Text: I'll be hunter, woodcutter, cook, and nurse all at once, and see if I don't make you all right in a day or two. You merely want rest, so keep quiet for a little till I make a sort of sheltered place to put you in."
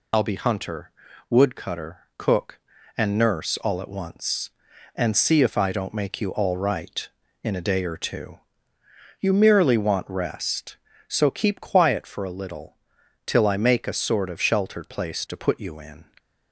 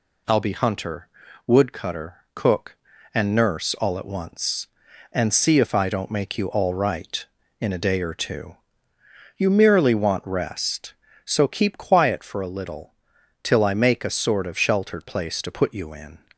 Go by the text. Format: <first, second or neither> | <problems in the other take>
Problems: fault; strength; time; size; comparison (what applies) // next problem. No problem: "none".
second | loses the start of "I'll"; at 0.1 s; 35 ms // pauses between "little" and "till"; noticeable; at 12.7 s; 0.50 s long; noticeable in the second